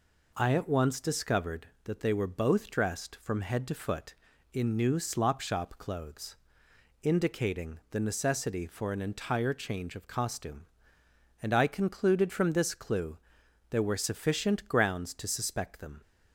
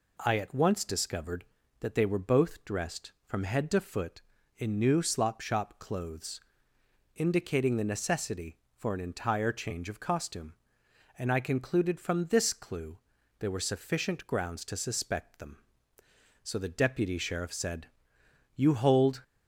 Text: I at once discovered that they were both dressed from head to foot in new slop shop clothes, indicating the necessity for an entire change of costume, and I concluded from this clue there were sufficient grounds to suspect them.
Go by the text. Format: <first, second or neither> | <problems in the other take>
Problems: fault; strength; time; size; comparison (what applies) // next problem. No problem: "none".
first | pauses between "clue" and "there"; at 12.9 s; 0.42 s long; noticeable in the first // goes on to say "So the deputy sheriff said You hold"; strong; from 16.4 s on; 2.8 s long